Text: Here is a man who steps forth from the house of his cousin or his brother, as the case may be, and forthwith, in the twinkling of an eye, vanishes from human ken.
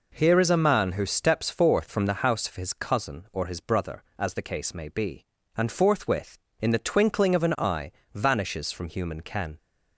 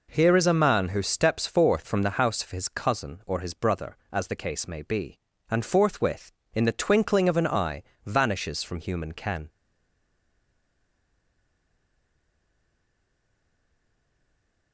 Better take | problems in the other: first | stays silent after the last word; strong; from 9.4 s on; 5.3 s long

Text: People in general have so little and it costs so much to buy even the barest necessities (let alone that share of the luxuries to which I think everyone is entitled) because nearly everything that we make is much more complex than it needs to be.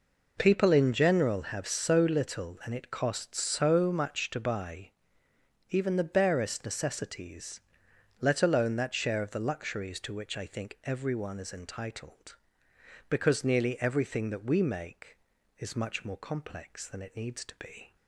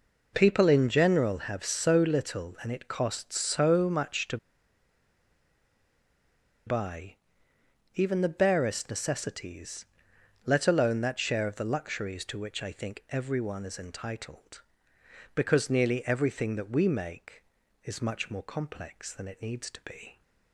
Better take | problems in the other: first | pauses between "to" and "buy"; strong; at 4.3 s; 2.3 s long // pauses between "buy" and "even"; noticeable; at 7.1 s; 0.80 s long; noticeable in the first

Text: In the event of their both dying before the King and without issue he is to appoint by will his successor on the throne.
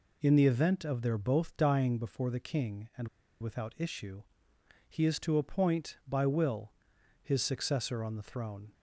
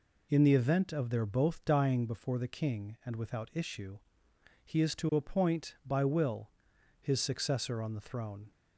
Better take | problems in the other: second | pauses between "and" and "without"; slight; at 3.0 s; 0.32 s long // pauses between "issue" and "he"; noticeable; at 4.2 s; 0.68 s long; noticeable in the second // pauses between "will" and "his"; noticeable; at 6.7 s; 0.50 s long; noticeable in the second

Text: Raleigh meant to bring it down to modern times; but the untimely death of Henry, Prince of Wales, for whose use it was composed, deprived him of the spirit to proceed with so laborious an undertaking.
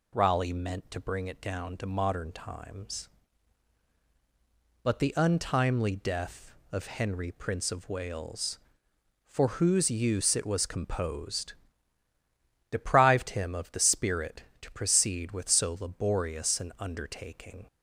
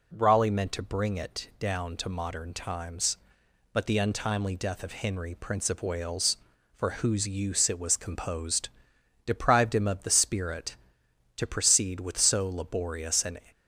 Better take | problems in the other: first | stops before "undertaking"; at 13.5 s

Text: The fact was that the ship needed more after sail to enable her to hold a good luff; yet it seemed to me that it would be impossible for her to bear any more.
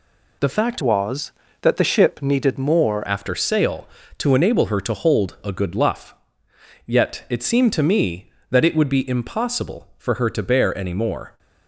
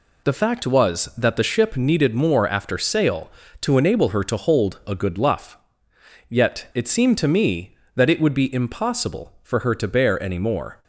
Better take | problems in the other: second | changes voice from "was" to "more"; from 0.8 to 3.0 s; 2.2 s long

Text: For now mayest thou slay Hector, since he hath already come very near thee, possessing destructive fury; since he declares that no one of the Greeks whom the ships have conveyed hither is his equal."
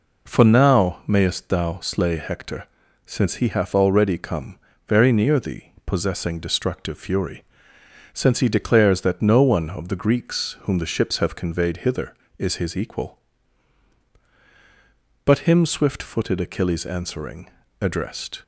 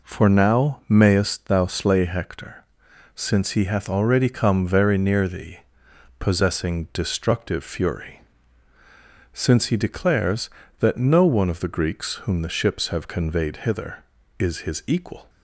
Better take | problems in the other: second | pauses between "come" and "very"; slight; at 4.5 s; 0.28 s long // goes on to say "But him swift footed Achilles answering addressed"; strong; from 15.2 s on; 3.1 s long

